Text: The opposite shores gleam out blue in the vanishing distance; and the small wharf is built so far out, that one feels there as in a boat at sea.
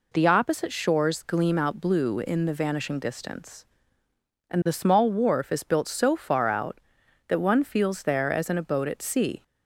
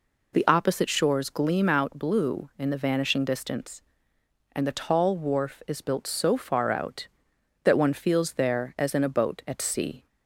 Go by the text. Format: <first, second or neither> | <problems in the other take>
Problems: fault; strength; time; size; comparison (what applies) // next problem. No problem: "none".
first | says "tall" for "small"; at 4.7 s